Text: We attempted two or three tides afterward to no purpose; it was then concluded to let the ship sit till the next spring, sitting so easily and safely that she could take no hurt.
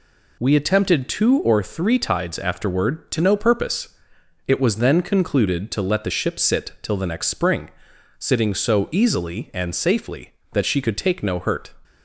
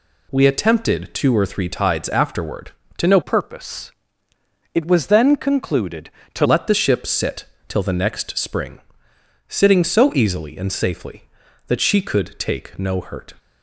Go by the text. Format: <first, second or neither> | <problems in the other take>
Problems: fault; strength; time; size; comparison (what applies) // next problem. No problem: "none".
first | changes voice from "purpose" to "to"; from 3.2 to 6.4 s; 3.2 s long // pauses between "sit" and "till"; slight; at 7.4 s; 0.24 s long